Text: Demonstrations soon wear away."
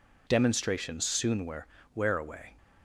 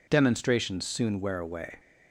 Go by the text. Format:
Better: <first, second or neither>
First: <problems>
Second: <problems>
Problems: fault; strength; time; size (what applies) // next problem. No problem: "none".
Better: second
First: says "wear" twice; at 1.9 s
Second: none